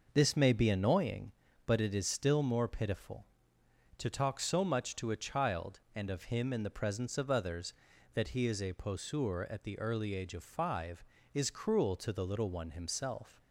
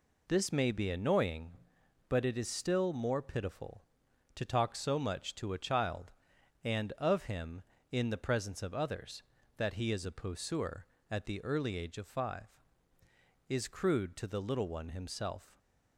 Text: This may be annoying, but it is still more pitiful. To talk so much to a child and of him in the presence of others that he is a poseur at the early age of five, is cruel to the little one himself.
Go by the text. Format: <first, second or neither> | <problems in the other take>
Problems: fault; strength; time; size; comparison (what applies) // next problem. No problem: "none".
first | says "crude" for "cruel"; at 13.6 s